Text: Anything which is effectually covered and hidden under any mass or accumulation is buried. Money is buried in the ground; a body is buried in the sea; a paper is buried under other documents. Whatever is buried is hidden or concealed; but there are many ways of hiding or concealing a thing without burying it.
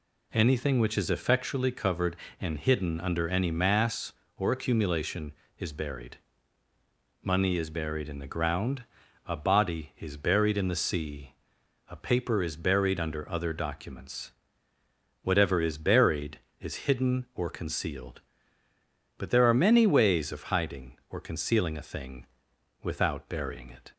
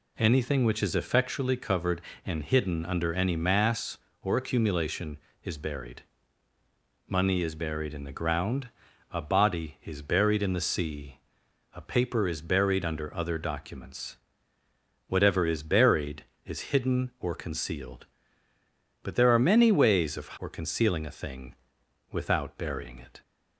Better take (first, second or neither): first